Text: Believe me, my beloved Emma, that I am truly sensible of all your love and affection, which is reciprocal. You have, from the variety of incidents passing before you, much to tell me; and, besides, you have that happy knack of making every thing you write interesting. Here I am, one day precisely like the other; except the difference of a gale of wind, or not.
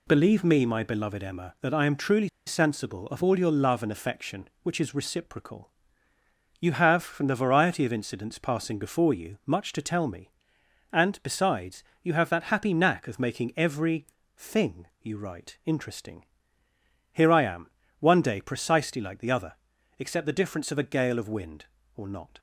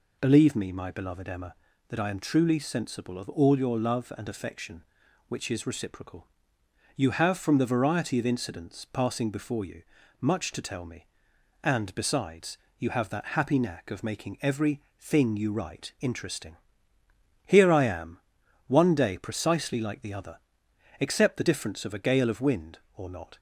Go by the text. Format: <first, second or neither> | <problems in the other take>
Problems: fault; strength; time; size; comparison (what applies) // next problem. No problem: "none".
second | pauses between "truly" and "sensible"; slight; at 2.2 s; 0.17 s long // pauses between "every" and "thing"; slight; at 14.0 s; 0.28 s long; slight in the second